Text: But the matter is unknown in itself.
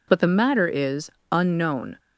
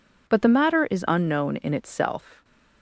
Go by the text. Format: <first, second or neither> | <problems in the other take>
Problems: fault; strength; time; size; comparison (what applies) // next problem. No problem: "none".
second | pauses between "is" and "unknown"; slight; at 1.1 s; 0.20 s long // stops before "in itself"; at 1.9 s